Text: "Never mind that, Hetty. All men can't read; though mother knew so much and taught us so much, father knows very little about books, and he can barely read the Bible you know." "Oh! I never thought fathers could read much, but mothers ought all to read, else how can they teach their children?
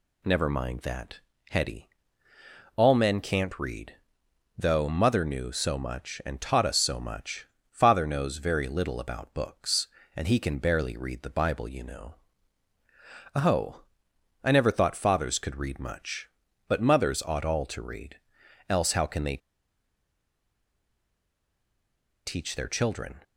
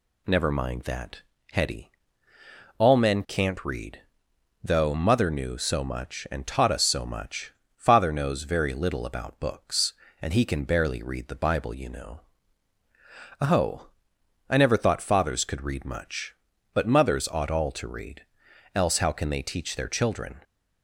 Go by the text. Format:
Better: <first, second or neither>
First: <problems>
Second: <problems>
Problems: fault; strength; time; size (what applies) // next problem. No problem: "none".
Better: second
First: pauses between "they" and "teach"; strong; at 19.3 s; 2.8 s long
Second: none